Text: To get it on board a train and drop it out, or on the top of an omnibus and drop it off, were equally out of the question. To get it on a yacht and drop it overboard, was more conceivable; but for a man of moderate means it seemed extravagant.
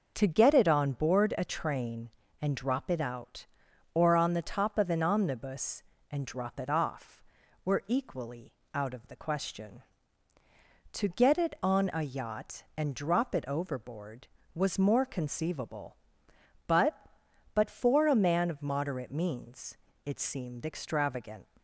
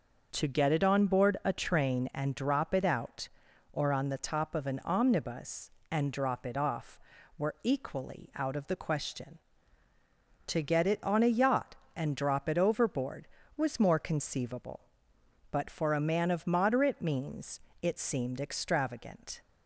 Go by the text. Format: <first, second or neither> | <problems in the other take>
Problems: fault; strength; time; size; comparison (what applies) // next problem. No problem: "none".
second | starts louder than the rest; noticeable; until 1.1 s; 6 dB; also in the second // pauses between "equally" and "out"; slight; at 8.5 s; 0.22 s long // says "but" twice; at 17.5 s // pauses between "means" and "it"; slight; at 19.7 s; 0.26 s long; slight in the second